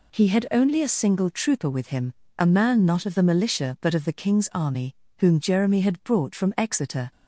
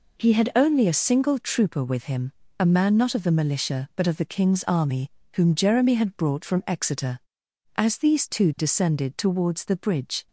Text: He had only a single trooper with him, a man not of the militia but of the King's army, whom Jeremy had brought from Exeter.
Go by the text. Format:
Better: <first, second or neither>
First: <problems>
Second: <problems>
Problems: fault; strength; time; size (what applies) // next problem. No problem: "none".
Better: first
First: none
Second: goes on to say "As these two descended towards the bridge"; strong; from 7.7 s on; 2.5 s long